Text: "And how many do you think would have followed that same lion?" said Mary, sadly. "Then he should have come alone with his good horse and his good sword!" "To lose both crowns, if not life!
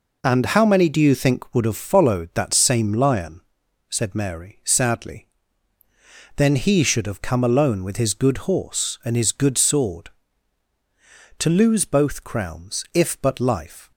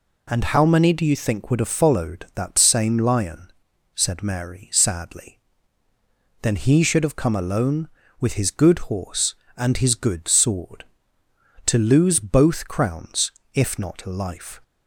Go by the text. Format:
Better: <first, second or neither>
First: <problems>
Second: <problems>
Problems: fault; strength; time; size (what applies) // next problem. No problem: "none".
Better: second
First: says "but" for "not"; at 13.2 s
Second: none